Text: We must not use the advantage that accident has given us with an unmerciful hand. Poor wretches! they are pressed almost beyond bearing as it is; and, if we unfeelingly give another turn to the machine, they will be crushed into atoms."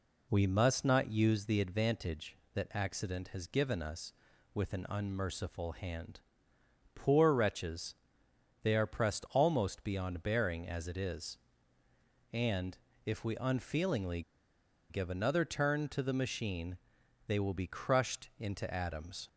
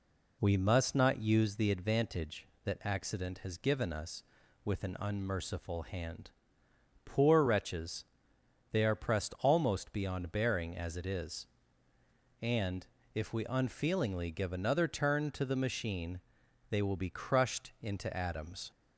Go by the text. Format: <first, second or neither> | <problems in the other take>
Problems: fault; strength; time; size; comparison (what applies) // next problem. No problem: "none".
second | pauses between "unfeelingly" and "give"; noticeable; at 14.2 s; 0.68 s long